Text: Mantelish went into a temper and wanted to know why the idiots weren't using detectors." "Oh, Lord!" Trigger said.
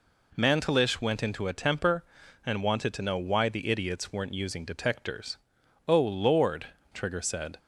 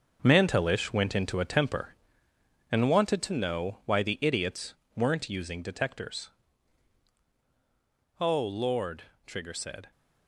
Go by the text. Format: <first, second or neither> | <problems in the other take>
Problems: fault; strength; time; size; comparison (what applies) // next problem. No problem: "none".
first | gets quieter; strong; throughout; 8 dB // pauses between "idiots" and "weren't"; slight; at 4.7 s; 0.22 s long